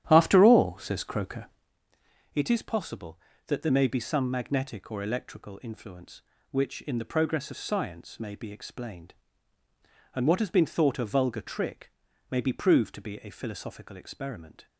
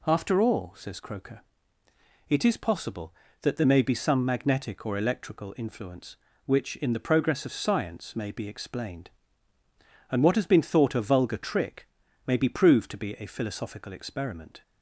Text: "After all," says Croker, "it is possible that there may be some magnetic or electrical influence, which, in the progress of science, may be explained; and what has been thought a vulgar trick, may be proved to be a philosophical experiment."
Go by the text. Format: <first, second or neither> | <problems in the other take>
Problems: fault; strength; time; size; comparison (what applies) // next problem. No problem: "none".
second | starts louder than the rest; strong; until 1.7 s; 11 dB